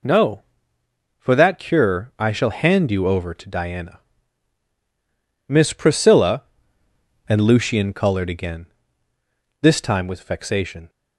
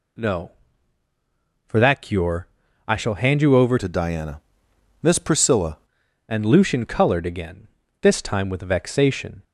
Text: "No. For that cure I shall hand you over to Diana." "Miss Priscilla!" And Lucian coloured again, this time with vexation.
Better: first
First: none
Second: pauses between "cure" and "I"; at 2.4 s; 0.40 s long // changes voice from "to" to "Priscilla"; from 3.7 to 5.7 s; 2.0 s long

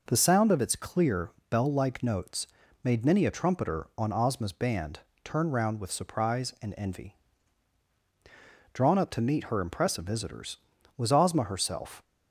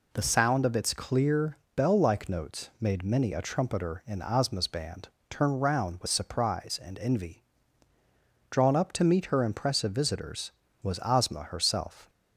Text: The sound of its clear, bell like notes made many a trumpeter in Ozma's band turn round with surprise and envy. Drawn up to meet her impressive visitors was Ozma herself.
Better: second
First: pauses between "notes" and "made"; at 2.4 s; 0.38 s long // says "on" for "in"; at 3.9 s // pauses between "band" and "turn"; slight; at 4.9 s; 0.24 s long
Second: pauses between "band" and "turn"; slight; at 5.0 s; 0.20 s long

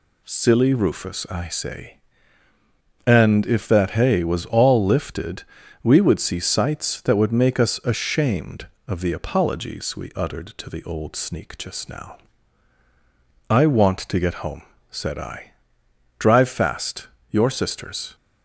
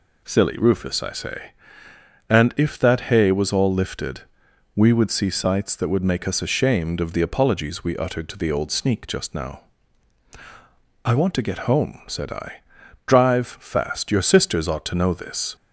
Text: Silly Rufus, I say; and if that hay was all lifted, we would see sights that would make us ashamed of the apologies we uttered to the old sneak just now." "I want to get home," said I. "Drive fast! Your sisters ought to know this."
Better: second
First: stops before "ought to know this"; at 18.1 s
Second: none

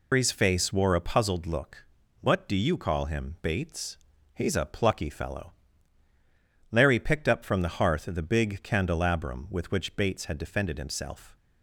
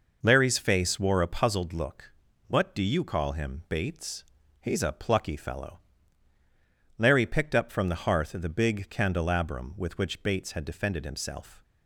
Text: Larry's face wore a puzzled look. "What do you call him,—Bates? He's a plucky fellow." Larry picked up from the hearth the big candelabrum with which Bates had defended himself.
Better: second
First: loses the start of "Larry's"; at 0.1 s; 160 ms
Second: none

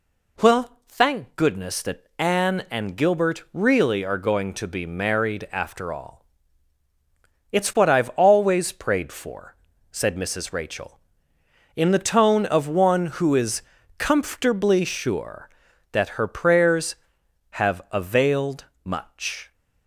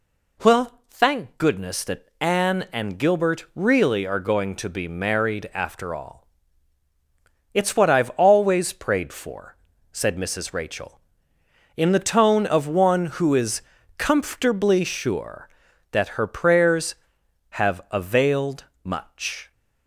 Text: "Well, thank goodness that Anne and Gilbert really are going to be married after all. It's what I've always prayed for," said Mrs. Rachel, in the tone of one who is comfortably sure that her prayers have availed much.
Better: neither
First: pauses between "is" and "comfortably"; slight; at 13.6 s; 0.36 s long // pauses between "availed" and "much"; slight; at 18.6 s; 0.20 s long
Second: pauses between "is" and "comfortably"; slight; at 13.6 s; 0.36 s long // pauses between "availed" and "much"; slight; at 18.6 s; 0.20 s long

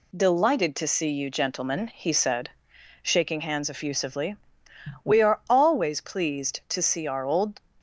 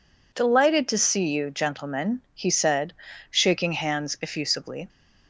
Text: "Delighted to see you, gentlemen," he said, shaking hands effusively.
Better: second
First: goes on to say "We are always pleased to see our old"; strong; from 5.0 s on; 2.5 s long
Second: none

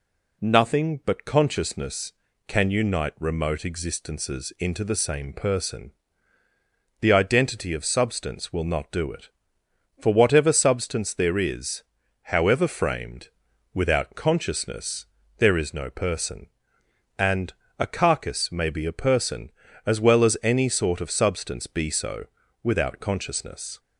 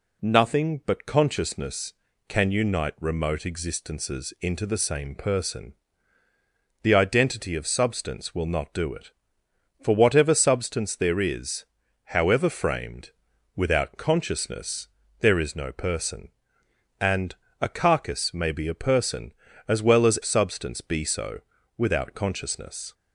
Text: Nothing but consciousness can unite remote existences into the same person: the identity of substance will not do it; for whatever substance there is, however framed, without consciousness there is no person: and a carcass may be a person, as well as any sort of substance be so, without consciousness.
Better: first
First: pauses between "consciousness" and "there"; slight; at 15.0 s; 0.30 s long // pauses between "and" and "a"; slight; at 17.5 s; 0.26 s long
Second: pauses between "consciousness" and "there"; slight; at 14.8 s; 0.30 s long // pauses between "and" and "a"; slight; at 17.3 s; 0.26 s long // skips "any sort of"; at 20.2 s

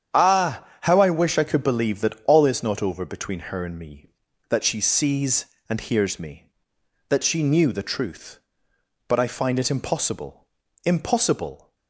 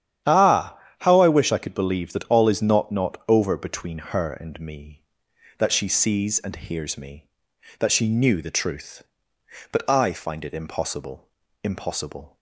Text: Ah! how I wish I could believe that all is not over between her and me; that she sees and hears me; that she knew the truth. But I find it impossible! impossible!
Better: first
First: starts louder than the rest; strong; until 1.2 s; 8.5 dB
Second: starts louder than the rest; strong; until 1.4 s; 10 dB // says "not" twice; at 2.9 s

